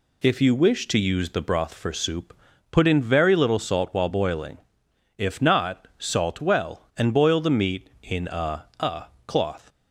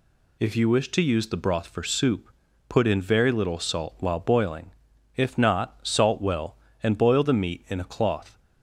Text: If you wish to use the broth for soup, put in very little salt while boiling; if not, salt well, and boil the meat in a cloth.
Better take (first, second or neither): second